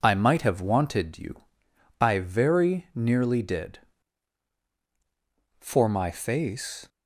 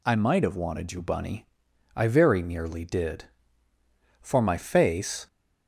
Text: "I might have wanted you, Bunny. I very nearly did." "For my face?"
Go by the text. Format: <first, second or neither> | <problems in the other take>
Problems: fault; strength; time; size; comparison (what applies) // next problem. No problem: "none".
second | skips "Bunny"; at 1.7 s